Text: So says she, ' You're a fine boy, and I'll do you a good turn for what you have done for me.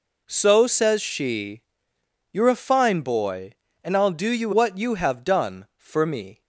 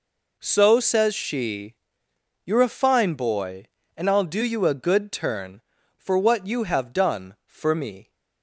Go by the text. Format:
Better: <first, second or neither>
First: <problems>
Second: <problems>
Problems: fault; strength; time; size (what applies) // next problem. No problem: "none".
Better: second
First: skips "a good turn for"; at 4.5 s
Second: none